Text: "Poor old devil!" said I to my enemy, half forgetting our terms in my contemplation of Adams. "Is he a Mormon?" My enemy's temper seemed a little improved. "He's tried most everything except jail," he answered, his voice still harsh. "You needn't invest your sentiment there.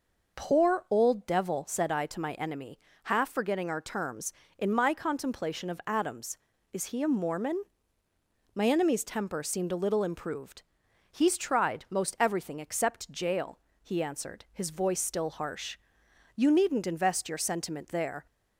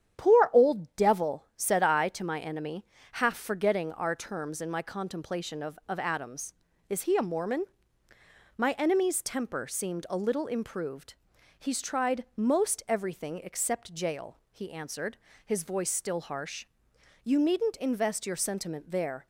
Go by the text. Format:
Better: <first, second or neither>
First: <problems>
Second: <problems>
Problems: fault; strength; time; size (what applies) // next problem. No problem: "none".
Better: first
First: none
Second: starts louder than the rest; strong; until 1.2 s; 9 dB // says "of" twice; at 5.8 s